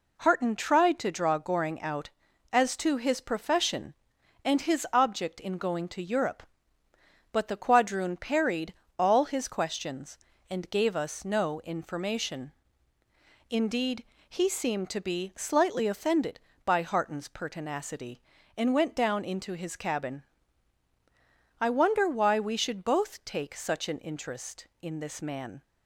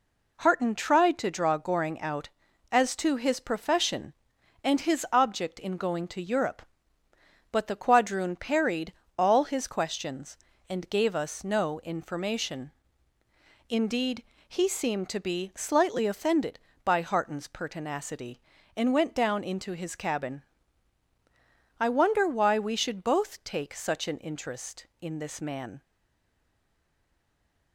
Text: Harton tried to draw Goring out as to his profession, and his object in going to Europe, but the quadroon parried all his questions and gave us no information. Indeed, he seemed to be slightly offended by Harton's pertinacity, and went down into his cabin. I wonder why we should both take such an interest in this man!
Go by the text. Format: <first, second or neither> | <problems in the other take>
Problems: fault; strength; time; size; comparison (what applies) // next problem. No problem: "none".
first | pauses between "parried" and "all"; slight; at 8.9 s; 0.24 s long; slight in the first // stays silent after the last word; noticeable; from 25.8 s on; 1.9 s long